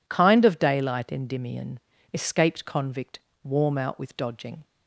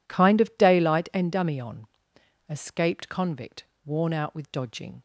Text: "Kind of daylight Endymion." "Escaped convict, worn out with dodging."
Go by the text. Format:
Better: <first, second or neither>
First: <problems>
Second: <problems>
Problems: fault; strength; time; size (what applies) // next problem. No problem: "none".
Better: second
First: says "warm" for "worn"; at 3.4 s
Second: none